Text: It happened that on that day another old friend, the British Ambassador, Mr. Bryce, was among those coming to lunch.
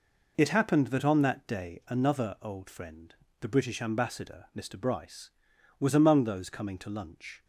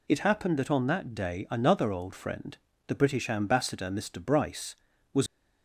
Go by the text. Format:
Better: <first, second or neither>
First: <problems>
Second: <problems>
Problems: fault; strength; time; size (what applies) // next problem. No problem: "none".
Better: first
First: none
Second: stops before "among those coming to lunch"; at 5.2 s